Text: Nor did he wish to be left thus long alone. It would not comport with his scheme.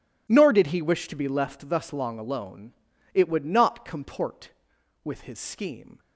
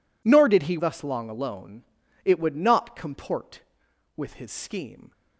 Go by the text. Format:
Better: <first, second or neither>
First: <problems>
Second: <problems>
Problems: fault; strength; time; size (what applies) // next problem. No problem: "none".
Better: first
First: none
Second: skips "wish to be left"; at 0.7 s